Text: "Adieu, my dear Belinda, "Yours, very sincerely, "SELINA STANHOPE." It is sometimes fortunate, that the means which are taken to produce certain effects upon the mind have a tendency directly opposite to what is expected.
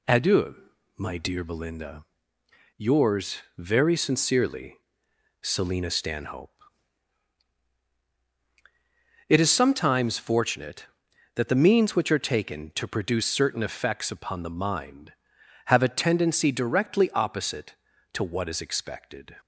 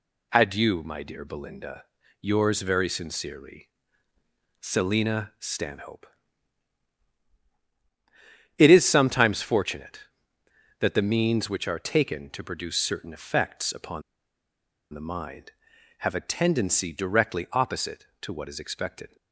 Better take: first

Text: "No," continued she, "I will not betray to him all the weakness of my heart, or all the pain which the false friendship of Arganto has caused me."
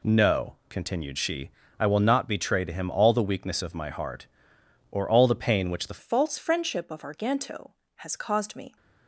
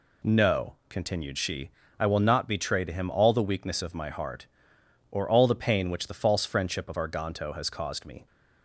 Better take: second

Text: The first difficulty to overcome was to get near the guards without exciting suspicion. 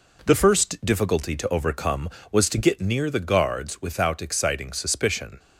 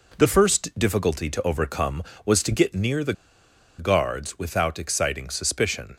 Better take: first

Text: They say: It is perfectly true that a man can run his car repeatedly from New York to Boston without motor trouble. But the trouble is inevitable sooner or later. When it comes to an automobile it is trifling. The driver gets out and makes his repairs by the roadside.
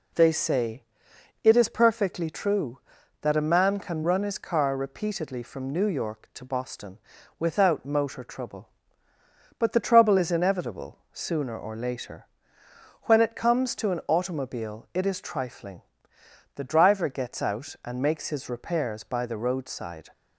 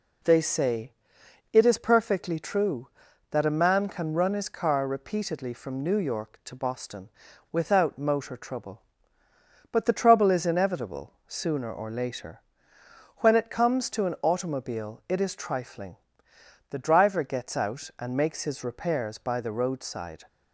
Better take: neither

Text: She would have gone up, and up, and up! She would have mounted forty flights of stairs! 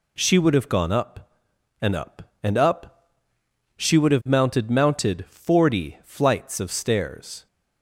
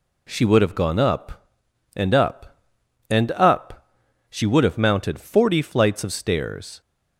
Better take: second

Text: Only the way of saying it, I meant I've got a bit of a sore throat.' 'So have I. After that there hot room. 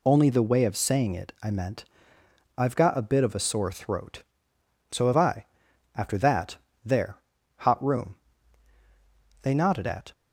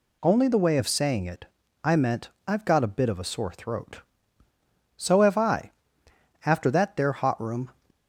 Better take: second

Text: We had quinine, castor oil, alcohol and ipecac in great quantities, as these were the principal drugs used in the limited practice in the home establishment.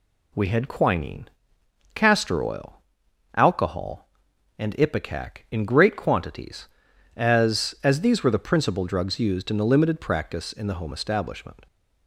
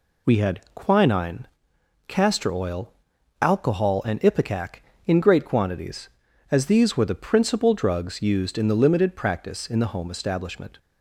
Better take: second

